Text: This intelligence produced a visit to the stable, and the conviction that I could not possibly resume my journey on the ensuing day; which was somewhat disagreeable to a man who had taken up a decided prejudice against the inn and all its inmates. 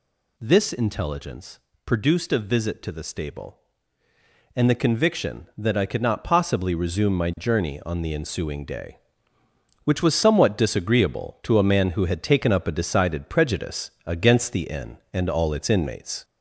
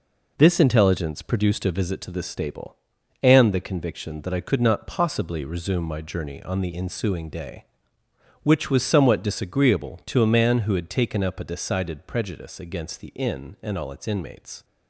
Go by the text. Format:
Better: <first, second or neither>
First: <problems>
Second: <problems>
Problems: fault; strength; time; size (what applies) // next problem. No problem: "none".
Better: second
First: gets louder; throughout; 3.5 dB // pauses between "intelligence" and "produced"; slight; at 1.5 s; 0.28 s long // pauses between "prejudice" and "against"; slight; at 13.9 s; 0.16 s long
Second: none